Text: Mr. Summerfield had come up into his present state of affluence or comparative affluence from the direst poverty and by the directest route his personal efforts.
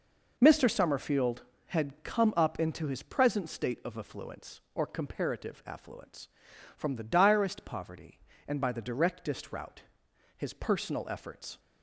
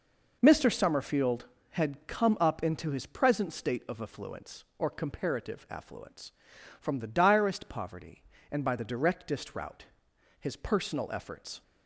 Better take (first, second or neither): neither